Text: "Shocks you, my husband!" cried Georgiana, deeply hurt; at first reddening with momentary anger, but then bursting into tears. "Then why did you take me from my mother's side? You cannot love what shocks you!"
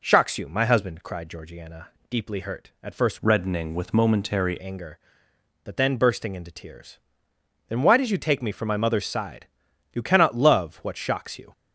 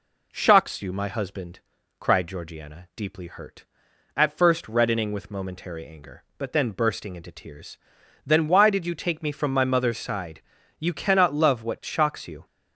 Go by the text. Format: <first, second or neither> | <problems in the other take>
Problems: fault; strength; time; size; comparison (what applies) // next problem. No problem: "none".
second | changes voice from "reddening" to "momentary"; from 3.2 to 4.5 s; 1.3 s long